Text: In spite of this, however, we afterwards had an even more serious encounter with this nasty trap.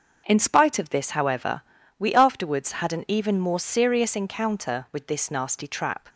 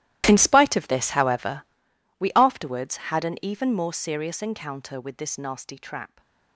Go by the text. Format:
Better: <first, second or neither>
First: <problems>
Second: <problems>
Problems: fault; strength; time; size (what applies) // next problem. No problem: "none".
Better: first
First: starts louder than the rest; until 1.2 s; 6.5 dB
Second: gets quieter; strong; throughout; 17.5 dB // starts louder than the rest; strong; until 1.2 s; 14.5 dB